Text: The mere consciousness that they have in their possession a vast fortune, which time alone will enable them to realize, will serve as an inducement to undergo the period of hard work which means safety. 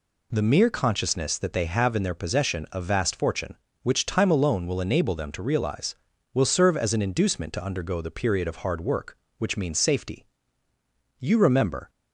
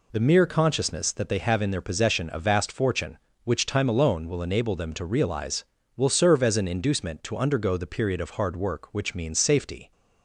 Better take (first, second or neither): second